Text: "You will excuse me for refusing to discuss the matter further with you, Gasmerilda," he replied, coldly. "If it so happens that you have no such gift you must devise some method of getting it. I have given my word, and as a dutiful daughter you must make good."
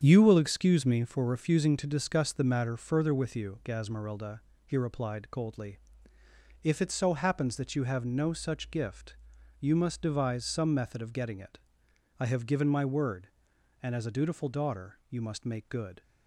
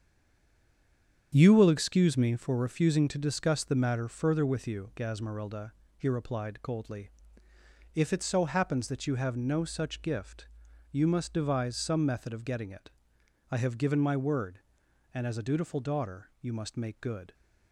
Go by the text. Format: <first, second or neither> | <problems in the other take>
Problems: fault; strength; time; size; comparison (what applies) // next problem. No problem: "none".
first | stays silent before the first word; noticeable; until 1.3 s; 1.3 s long // starts louder than the rest; strong; until 2.4 s; 7.5 dB; strong in the first // pauses between "gift" and "you"; noticeable; at 10.4 s; 0.46 s long; noticeable in the first